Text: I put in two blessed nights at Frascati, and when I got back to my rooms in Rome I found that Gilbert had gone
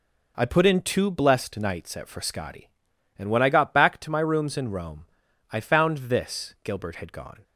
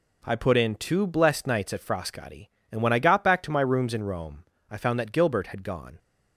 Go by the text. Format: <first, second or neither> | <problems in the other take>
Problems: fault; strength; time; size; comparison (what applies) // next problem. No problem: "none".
second | pauses between "Rome" and "I"; at 5.0 s; 0.44 s long; slight in the second // says "this" for "that"; at 6.0 s